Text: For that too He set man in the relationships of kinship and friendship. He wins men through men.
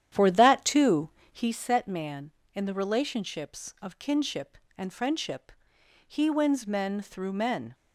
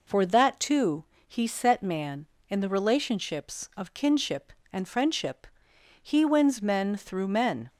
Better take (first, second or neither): second